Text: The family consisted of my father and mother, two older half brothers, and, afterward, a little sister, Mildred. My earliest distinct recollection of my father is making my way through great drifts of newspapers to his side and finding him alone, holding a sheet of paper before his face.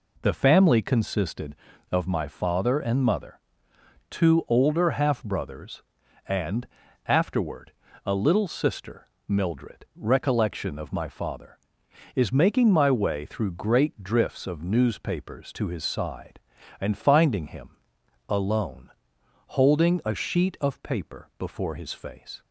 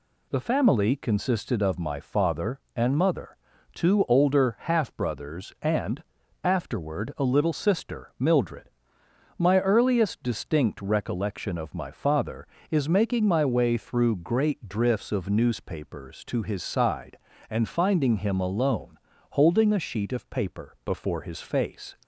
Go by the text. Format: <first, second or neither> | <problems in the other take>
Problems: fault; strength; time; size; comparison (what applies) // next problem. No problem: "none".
second | skips "My earliest distinct"; at 9.8 s // pauses between "him" and "alone"; noticeable; at 17.7 s; 0.58 s long